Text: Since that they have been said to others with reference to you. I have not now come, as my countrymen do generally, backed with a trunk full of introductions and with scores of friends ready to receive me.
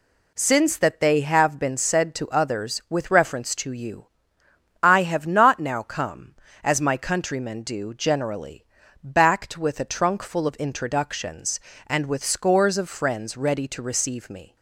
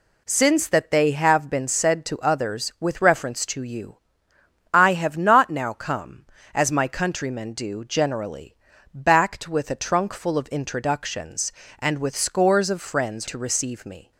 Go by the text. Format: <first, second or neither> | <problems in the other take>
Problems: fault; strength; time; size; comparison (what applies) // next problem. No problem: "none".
first | skips "ready"; at 13.2 s